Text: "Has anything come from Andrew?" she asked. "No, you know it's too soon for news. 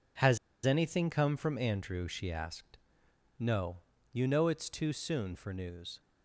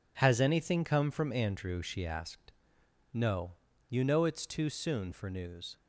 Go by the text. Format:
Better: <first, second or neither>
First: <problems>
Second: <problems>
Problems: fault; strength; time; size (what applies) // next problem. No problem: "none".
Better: second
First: pauses between "Has" and "anything"; slight; at 0.3 s; 0.27 s long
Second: none